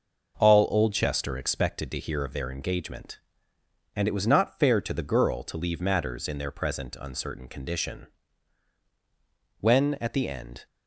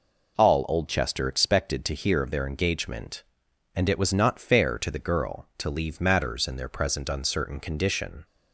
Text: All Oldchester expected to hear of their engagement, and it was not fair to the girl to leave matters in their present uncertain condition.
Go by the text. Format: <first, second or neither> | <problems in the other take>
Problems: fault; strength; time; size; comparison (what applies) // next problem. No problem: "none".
second | goes on to say "When at the end"; noticeable; from 9.6 s on; 1.0 s long